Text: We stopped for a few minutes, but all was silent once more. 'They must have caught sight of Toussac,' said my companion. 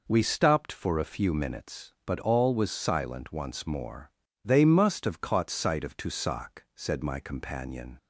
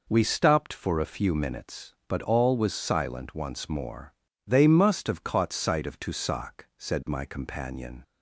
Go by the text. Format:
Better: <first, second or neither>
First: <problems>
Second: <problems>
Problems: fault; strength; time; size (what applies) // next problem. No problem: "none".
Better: neither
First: none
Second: none